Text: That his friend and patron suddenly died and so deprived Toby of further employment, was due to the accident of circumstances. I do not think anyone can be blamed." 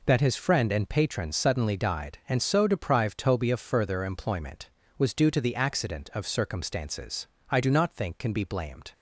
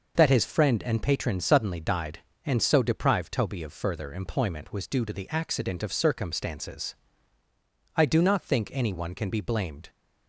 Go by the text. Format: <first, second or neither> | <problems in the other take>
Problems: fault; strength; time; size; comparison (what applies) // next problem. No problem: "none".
second | skips "anyone"; at 8.1 s